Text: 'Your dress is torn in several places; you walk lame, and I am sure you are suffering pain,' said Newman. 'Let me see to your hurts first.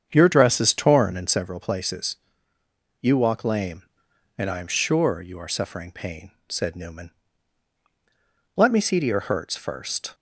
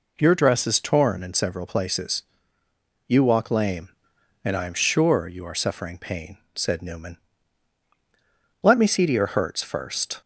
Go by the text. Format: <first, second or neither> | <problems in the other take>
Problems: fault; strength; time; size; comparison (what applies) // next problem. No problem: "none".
second | starts louder than the rest; strong; until 1.5 s; 7.5 dB